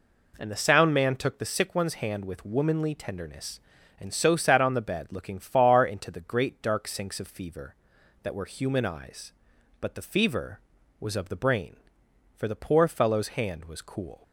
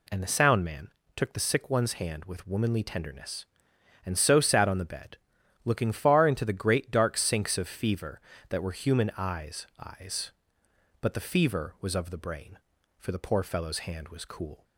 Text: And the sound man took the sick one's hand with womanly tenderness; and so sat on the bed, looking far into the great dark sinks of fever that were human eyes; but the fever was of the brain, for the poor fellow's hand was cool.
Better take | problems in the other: first | pauses between "man" and "took"; slight; at 0.8 s; 0.28 s long // says "eyes" twice; at 9.7 s

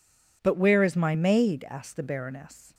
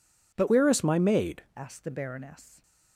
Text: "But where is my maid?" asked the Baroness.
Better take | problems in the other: first | changes voice from "where" to "maid"; from 0.4 to 1.4 s; 1.0 s long

